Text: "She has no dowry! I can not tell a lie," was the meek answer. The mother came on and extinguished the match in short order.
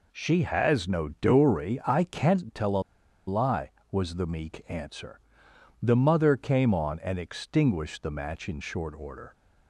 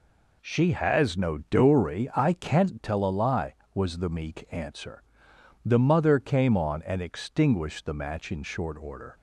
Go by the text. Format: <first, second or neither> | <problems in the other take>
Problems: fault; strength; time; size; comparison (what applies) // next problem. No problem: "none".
second | pauses between "a" and "lie"; at 2.8 s; 0.45 s long